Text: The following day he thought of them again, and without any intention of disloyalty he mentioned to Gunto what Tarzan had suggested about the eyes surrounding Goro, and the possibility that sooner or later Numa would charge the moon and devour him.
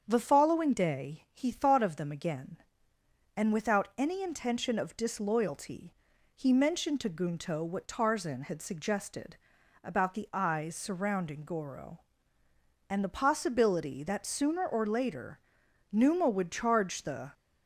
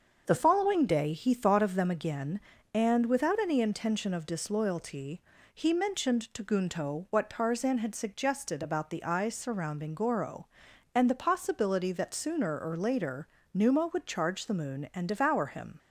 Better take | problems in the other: second | starts louder than the rest; strong; until 1.0 s; 7.5 dB; also in the second // pauses between "disloyalty" and "he"; at 5.9 s; 0.42 s long; slight in the second // pauses between "suggested" and "about"; noticeable; at 9.3 s; 0.46 s long // pauses between "later" and "Numa"; noticeable; at 15.3 s; 0.54 s long; slight in the second // stops before "moon and devour him"; at 17.3 s

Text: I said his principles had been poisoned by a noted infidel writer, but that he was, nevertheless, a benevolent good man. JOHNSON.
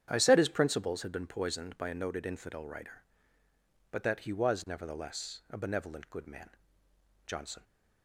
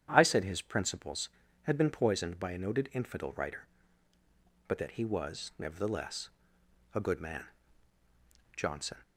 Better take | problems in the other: first | starts louder than the rest; strong; until 1.1 s; 9.5 dB; strong in the first // skips "benevolent"; at 7.0 s

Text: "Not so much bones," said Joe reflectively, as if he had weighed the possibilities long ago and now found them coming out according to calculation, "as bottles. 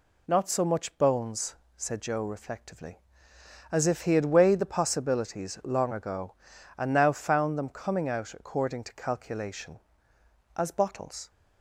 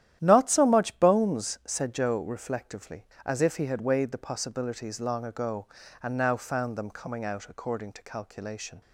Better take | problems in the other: first | starts louder than the rest; strong; until 1.2 s; 11.5 dB // stops before "as bottles"; at 8.8 s

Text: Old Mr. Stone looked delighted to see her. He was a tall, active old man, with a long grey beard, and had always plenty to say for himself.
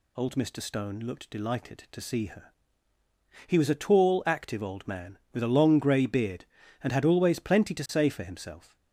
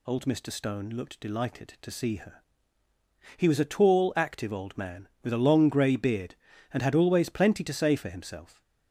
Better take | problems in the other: neither | none

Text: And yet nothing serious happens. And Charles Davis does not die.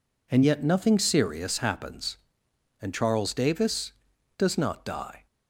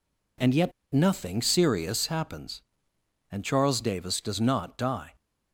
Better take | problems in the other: first | pauses between "yet" and "nothing"; slight; at 0.7 s; 0.21 s long

